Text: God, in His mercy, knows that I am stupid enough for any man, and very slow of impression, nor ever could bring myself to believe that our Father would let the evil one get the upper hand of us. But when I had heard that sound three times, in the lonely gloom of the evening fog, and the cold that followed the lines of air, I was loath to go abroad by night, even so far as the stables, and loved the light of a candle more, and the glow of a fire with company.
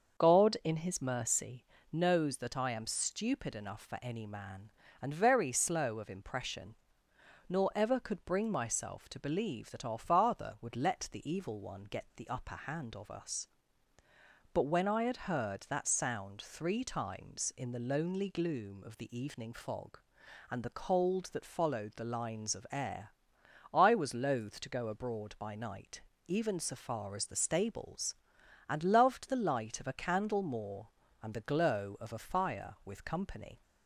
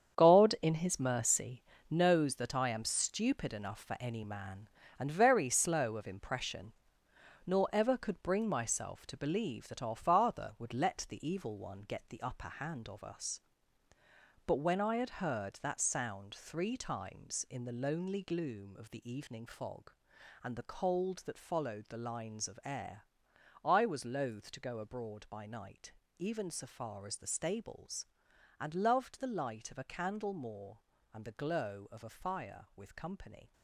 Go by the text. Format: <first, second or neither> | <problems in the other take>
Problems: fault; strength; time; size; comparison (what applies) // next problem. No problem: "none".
first | gets quieter; strong; throughout; 10 dB // starts louder than the rest; strong; until 1.2 s; 8 dB; also in the first